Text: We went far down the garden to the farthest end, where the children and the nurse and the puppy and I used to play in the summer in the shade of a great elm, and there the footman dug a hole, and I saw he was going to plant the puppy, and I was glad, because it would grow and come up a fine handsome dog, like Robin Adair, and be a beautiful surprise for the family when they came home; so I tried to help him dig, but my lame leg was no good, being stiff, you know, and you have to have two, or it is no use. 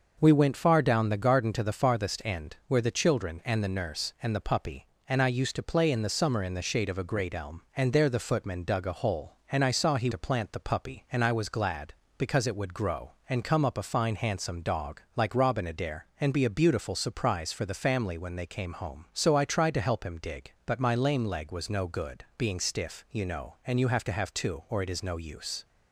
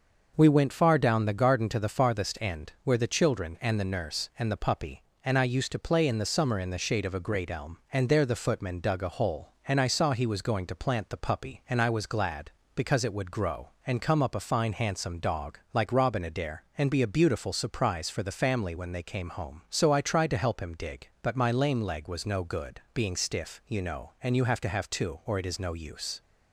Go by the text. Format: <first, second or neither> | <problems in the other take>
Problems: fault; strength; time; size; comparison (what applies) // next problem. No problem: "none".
second | skips "was going"; at 10.1 s